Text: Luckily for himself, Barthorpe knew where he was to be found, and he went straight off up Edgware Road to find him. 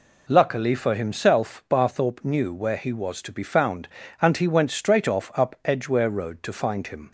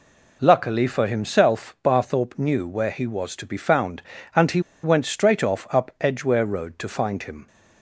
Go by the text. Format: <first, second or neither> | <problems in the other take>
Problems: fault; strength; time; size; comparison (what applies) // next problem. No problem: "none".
first | pauses between "he" and "went"; slight; at 4.5 s; 0.23 s long